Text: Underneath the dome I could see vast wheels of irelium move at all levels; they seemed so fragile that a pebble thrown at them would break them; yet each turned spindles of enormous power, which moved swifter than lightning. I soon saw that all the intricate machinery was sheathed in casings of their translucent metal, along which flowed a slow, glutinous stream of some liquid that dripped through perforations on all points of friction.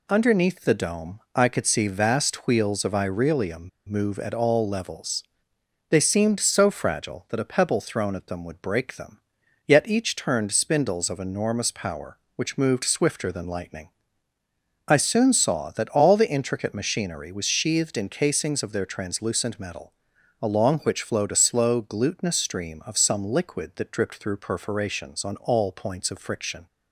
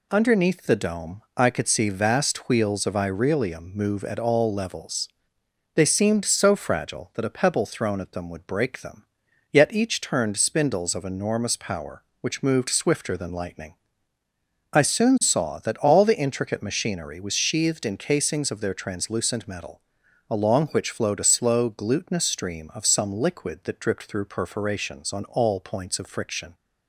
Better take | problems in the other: second | pauses between "irelium" and "move"; slight; at 3.6 s; 0.18 s long

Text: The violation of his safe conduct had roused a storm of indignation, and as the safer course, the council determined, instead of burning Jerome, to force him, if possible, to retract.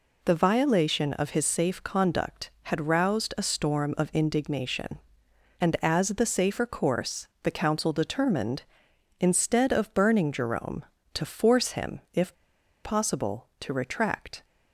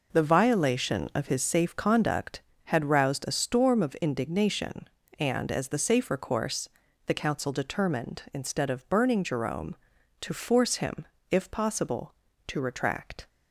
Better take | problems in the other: second | pauses between "if" and "possible"; noticeable; at 12.3 s; 0.48 s long

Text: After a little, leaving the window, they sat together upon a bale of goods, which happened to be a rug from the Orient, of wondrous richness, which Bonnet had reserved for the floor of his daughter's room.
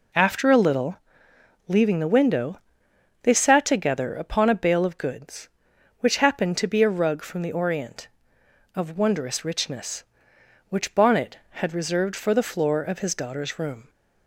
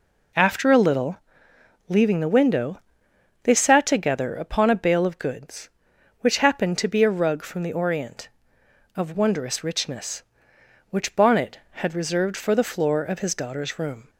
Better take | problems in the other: neither | none

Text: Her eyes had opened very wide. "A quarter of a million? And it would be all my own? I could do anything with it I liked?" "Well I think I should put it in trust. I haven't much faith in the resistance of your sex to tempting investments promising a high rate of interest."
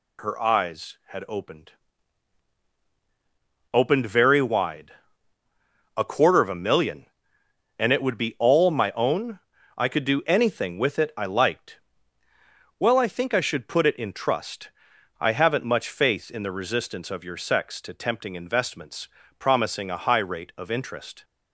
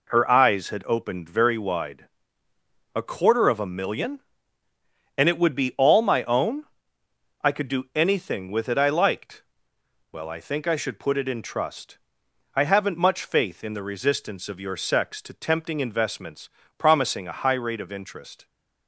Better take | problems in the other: second | says "opened" twice; at 3.7 s // pauses between "investments" and "promising"; slight; at 19.0 s; 0.30 s long; slight in the second

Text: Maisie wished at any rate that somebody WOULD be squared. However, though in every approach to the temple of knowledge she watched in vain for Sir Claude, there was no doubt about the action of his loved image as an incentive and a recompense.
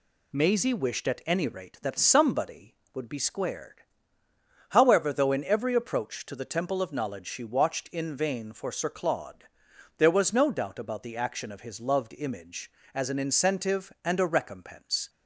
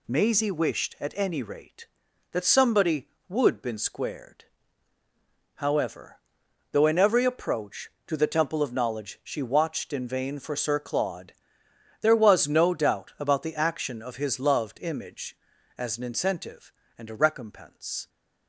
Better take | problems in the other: first | says "been" for "be"; at 3.6 s

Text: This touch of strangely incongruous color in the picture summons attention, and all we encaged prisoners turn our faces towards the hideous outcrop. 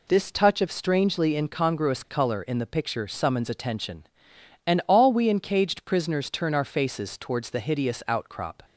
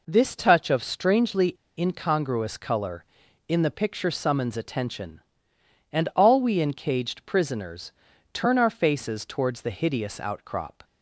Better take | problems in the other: first | pauses between "strangely" and "incongruous"; slight; at 1.5 s; 0.24 s long // pauses between "prisoners" and "turn"; at 7.9 s; 0.40 s long

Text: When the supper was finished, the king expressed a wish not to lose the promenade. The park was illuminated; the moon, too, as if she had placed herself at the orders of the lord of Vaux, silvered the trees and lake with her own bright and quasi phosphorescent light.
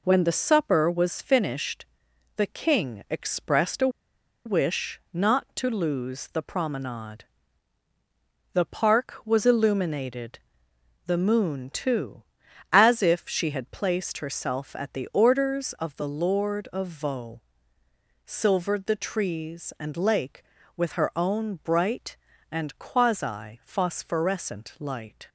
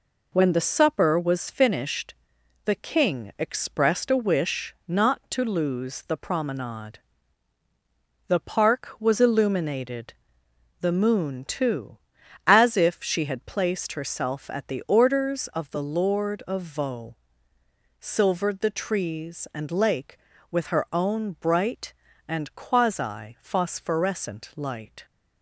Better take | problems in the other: second | pauses between "a" and "wish"; noticeable; at 3.8 s; 0.57 s long

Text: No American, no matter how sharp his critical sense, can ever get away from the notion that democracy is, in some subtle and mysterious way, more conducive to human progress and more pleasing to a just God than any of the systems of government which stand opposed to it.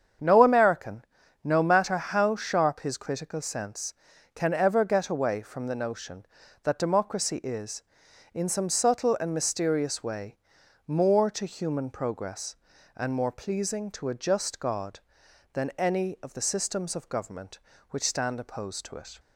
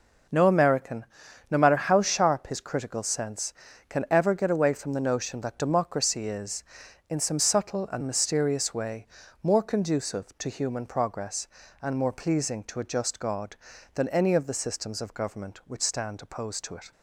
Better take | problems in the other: second | starts louder than the rest; strong; until 1.6 s; 7.5 dB // skips "conducive"; at 11.3 s

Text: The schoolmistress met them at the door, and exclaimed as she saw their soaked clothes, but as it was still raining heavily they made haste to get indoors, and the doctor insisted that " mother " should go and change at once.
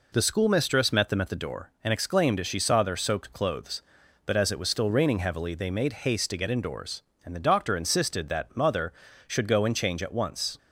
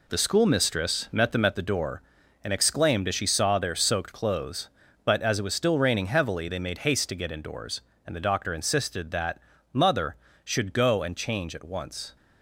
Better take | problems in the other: first | gets quieter; strong; throughout; 11 dB

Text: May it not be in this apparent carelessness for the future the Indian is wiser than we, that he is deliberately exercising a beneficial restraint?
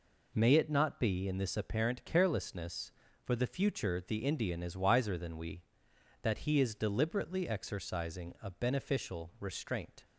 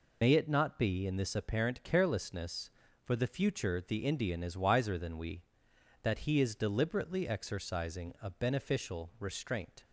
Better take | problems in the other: first | loses the start of "May"; at 0.2 s; 80 ms

